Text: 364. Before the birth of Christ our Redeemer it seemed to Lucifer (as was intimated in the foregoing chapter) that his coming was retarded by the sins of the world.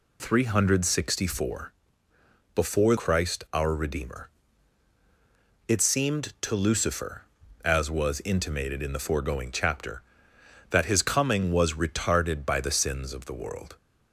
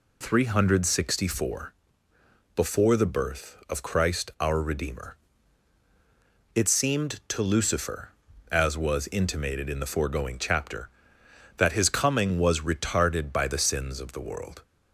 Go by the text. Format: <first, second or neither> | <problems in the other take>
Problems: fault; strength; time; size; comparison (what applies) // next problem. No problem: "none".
second | skips "the birth of"; at 2.9 s // pauses between "Redeemer" and "it"; strong; at 4.2 s; 1.3 s long; strong in the second